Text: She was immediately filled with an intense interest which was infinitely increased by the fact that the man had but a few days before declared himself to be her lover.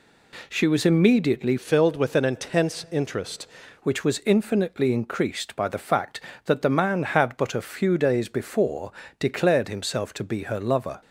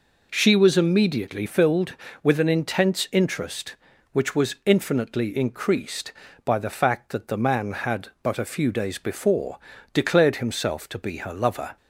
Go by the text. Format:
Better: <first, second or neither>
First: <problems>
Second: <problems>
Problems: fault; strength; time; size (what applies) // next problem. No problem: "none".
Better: second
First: changes voice from "filled" to "interest"; from 1.5 to 3.4 s; 1.9 s long // pauses between "before" and "declared"; slight; at 8.9 s; 0.28 s long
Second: pauses between "before" and "declared"; slight; at 9.5 s; 0.34 s long